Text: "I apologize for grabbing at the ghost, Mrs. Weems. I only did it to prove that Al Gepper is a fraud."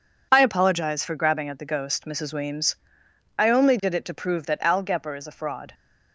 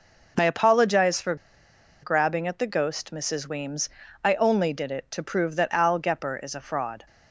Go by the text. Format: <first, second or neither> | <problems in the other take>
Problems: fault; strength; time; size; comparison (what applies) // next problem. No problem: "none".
first | pauses between "for" and "grabbing"; noticeable; at 1.3 s; 0.69 s long